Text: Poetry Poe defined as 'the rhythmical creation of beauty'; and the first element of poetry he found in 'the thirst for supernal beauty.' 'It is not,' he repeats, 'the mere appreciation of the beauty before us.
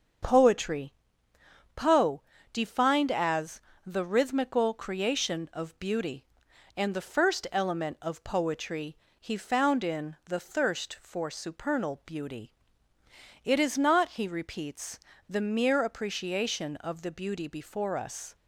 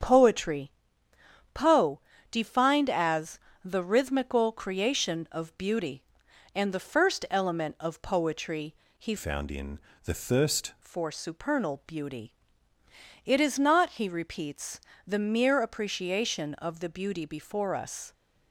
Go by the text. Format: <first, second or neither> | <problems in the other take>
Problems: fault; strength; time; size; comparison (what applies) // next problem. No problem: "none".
first | starts louder than the rest; strong; until 1.8 s; 8 dB; strong in the first // pauses between "Poetry" and "Poe"; noticeable; at 0.7 s; 0.82 s long; noticeable in the first // pauses between "Poe" and "defined"; slight; at 1.9 s; 0.32 s long; slight in the first // pauses between "as" and "the"; slight; at 3.3 s; 0.26 s long; slight in the first // pauses between "poetry" and "he"; slight; at 8.7 s; 0.24 s long; slight in the first // changes voice from "found" to "thirst"; from 9.1 to 10.7 s; 1.6 s long // pauses between "in" and "the"; slight; at 9.7 s; 0.24 s long